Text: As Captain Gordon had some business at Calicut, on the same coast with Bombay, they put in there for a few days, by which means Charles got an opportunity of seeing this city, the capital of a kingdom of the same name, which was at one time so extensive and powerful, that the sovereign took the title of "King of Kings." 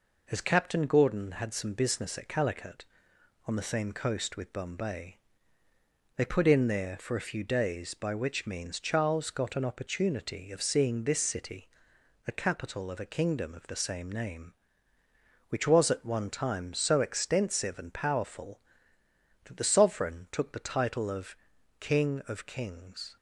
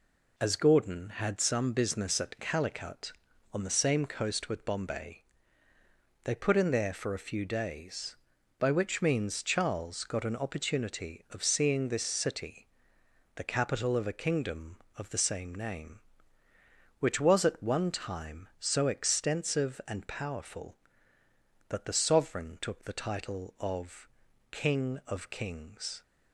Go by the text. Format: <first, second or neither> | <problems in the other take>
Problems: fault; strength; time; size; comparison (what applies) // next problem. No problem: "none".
first | skips "Captain"; at 0.5 s // pauses between "of" and "King"; at 24.0 s; 0.44 s long; also in the first